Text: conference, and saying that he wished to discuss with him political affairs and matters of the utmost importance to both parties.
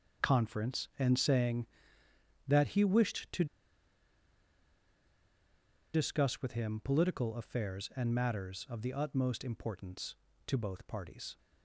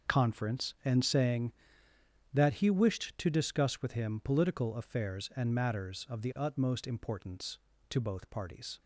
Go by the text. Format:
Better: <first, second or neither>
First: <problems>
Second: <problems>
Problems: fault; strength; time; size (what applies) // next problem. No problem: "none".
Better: second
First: starts louder than the rest; until 1.3 s; 6.5 dB // pauses between "to" and "discuss"; strong; at 3.4 s; 2.4 s long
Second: starts louder than the rest; until 1.1 s; 6.5 dB